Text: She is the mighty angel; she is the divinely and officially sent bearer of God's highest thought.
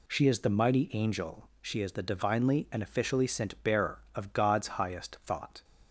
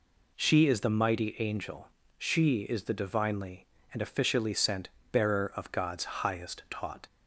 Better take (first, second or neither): first